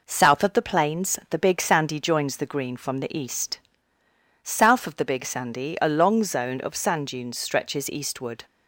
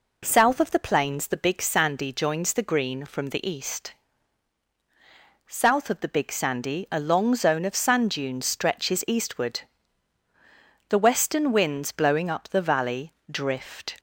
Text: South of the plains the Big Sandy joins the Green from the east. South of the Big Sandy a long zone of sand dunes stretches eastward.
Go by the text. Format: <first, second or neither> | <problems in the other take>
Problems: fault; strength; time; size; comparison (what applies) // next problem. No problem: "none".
first | goes on to say "The western winds blowing up the valley drift"; strong; from 10.8 s on; 3.1 s long